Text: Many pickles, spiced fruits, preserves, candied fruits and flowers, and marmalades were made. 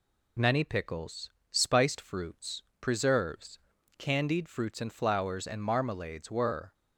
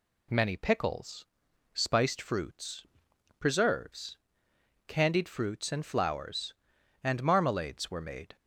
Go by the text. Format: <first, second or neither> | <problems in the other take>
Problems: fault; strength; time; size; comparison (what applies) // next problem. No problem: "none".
second | stops before "made"; at 6.7 s